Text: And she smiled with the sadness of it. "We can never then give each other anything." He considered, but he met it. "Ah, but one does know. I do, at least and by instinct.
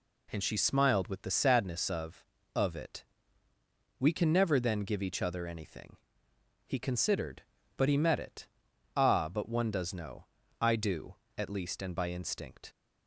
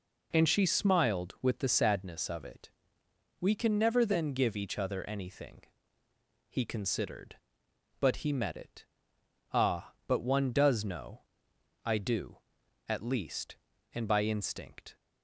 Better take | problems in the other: second | says "of" twice; at 2.5 s

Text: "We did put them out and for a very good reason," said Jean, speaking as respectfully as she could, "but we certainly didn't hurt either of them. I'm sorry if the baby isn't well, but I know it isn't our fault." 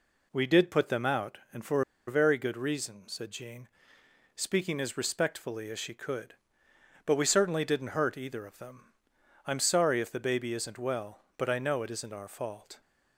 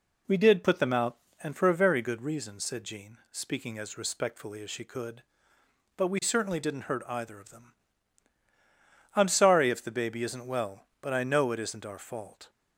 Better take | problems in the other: second | pauses between "for" and "a"; slight; at 1.8 s; 0.26 s long

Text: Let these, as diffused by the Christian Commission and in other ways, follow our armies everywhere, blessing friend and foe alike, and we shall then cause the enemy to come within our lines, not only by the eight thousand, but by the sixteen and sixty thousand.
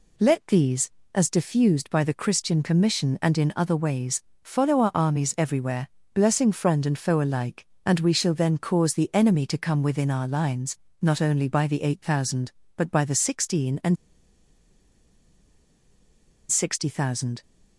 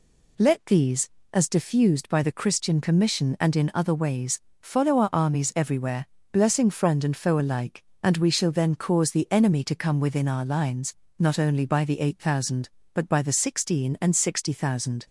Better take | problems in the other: second | pauses between "and" and "sixty"; strong; at 13.9 s; 2.5 s long

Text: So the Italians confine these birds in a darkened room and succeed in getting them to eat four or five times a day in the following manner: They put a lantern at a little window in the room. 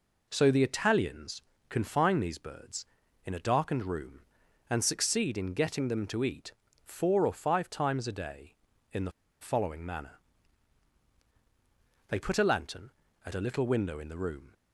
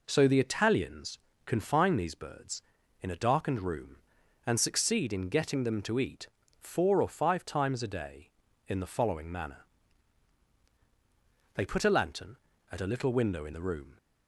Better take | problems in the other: second | pauses between "Italians" and "confine"; slight; at 1.4 s; 0.28 s long; slight in the second // pauses between "eat" and "four"; slight; at 6.5 s; 0.32 s long; slight in the second // pauses between "the" and "following"; slight; at 9.1 s; 0.29 s long

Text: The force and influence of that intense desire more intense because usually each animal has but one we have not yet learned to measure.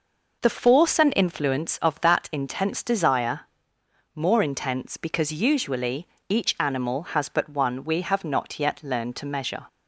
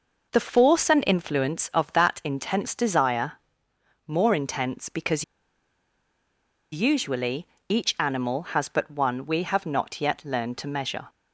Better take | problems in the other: first | pauses between "desire" and "more"; noticeable; at 3.3 s; 0.72 s long; noticeable in the first // pauses between "because" and "usually"; strong; at 5.2 s; 1.4 s long // pauses between "usually" and "each"; slight; at 7.4 s; 0.22 s long; slight in the first

